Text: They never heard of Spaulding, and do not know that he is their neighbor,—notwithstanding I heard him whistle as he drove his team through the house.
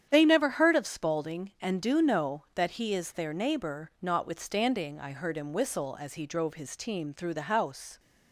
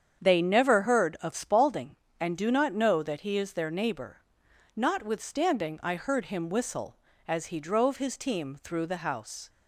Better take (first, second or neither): second